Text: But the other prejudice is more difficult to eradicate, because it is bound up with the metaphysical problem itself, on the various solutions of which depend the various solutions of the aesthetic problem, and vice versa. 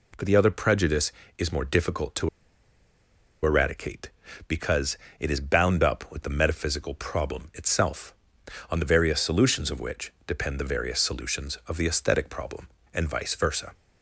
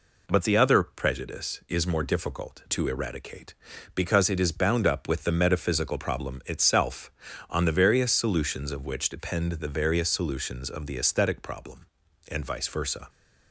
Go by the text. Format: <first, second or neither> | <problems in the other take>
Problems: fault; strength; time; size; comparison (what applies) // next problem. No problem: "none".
second | pauses between "to" and "eradicate"; at 2.2 s; 1.1 s long // pauses between "because" and "it"; slight; at 4.9 s; 0.22 s long